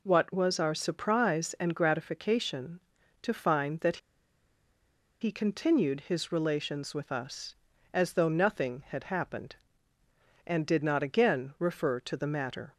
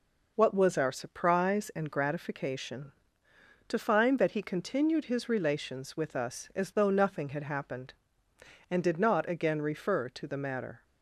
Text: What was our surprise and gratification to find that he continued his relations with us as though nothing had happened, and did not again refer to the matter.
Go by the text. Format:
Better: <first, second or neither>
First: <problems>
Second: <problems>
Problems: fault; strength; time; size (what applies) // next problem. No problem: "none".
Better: second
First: pauses between "that" and "he"; at 3.9 s; 1.2 s long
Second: none